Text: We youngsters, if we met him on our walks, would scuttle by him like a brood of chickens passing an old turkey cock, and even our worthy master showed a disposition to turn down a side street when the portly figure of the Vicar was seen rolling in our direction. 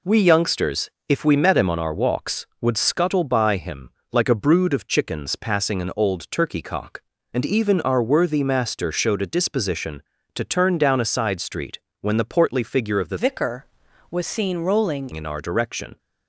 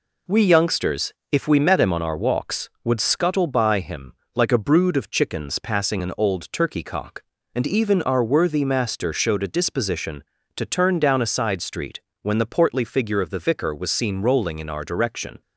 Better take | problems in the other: second | pauses between "him" and "like"; slight; at 3.8 s; 0.24 s long; slight in the second // pauses between "street" and "when"; slight; at 11.7 s; 0.24 s long; slight in the second // changes voice from "Vicar" to "rolling"; from 13.1 to 15.0 s; 1.9 s long

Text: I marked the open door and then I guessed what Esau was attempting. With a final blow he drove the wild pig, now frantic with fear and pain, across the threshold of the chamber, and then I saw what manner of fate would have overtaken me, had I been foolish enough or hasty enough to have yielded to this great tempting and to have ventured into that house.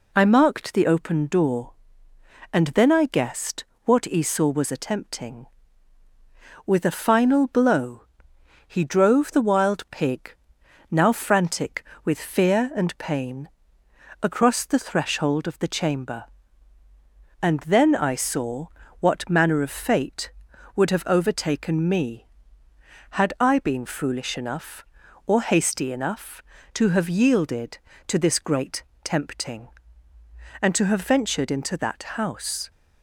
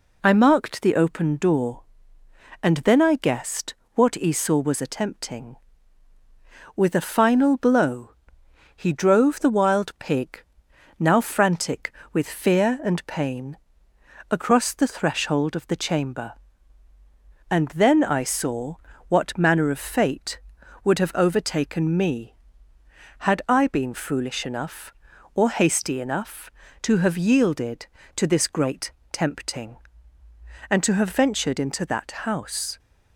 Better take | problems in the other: neither | pauses between "guessed" and "what"; slight; the same in both // pauses between "blow" and "he"; noticeable; the same in both // pauses between "saw" and "what"; slight; the same in both // pauses between "great" and "tempting"; slight; the same in both

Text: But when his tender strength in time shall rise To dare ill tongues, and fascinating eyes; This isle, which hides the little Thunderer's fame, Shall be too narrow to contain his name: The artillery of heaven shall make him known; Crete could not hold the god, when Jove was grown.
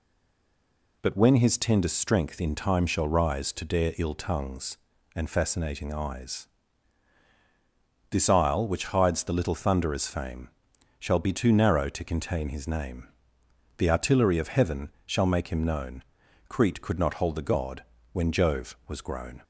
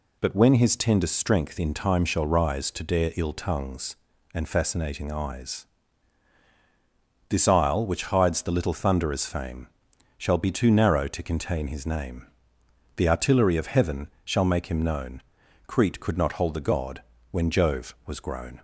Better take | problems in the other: second | stays silent before the first word; until 1.0 s; 1.0 s long // pauses between "heaven" and "shall"; slight; at 14.8 s; 0.16 s long; slight in the second

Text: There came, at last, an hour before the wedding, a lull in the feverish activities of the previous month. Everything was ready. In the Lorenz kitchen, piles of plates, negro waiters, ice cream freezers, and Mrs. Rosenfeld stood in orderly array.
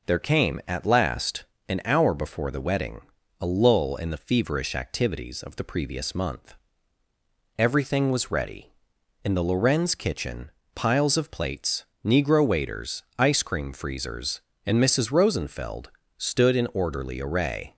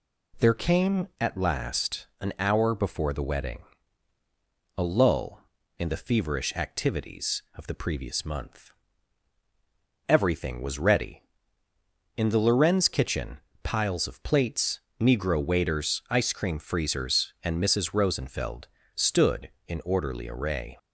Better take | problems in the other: neither | pauses between "Rosenfeld" and "stood"; slight; the same in both

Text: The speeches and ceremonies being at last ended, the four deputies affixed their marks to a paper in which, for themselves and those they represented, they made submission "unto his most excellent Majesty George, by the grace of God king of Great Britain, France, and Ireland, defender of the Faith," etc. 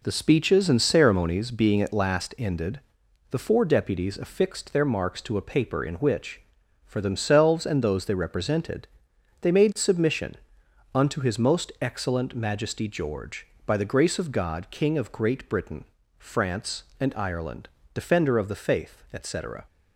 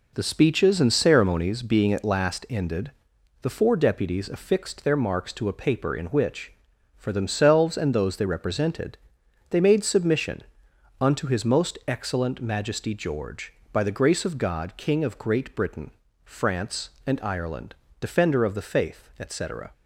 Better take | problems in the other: neither | pauses between "submission" and "unto"; noticeable; the same in both

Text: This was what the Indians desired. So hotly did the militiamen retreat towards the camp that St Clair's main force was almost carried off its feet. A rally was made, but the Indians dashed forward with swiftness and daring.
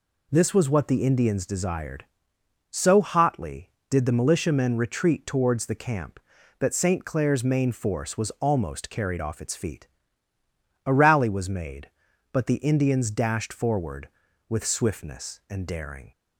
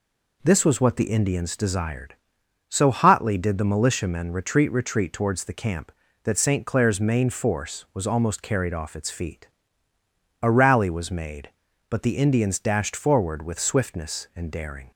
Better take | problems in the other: first | says "retreat" twice; at 4.7 s

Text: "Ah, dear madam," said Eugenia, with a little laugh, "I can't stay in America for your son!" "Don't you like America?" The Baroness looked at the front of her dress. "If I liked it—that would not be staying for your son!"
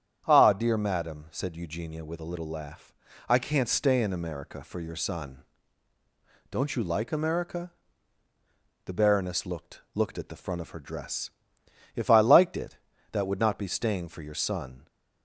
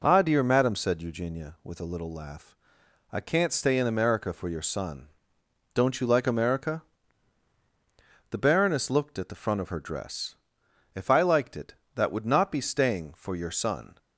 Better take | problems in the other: second | starts louder than the rest; strong; until 1.2 s; 9 dB // says "looked" twice; at 9.9 s

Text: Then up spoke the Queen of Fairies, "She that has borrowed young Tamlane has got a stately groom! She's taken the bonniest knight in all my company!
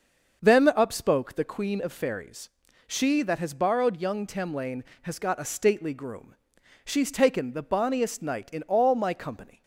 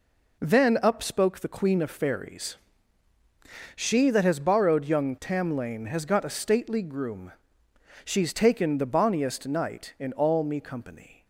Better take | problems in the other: first | says "me" for "my"; at 10.4 s

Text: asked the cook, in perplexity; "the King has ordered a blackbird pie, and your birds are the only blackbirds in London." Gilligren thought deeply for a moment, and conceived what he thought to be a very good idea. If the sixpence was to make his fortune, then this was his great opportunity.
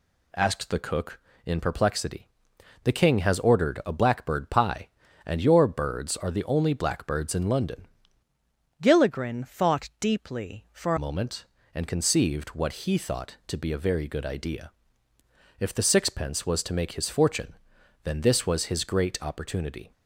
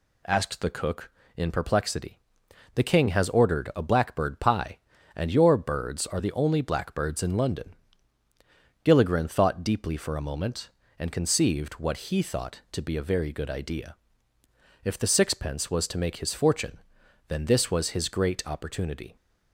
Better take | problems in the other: second | changes voice from "Gilligren" to "for"; from 8.8 to 10.9 s; 2.1 s long

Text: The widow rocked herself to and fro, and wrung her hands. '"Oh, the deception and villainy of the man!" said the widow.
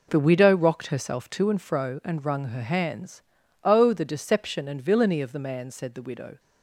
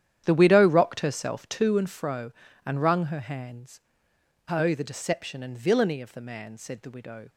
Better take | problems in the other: first | starts louder than the rest; strong; until 2.1 s; 10 dB

